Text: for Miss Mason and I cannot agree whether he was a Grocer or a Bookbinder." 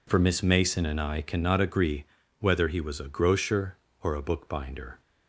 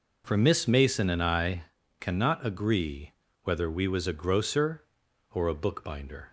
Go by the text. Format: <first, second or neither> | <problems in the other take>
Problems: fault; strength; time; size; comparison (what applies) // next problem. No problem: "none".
first | pauses between "I" and "cannot"; at 1.6 s; 0.38 s long // pauses between "agree" and "whether"; slight; at 3.1 s; 0.32 s long; slight in the first // says "we" for "he"; at 3.6 s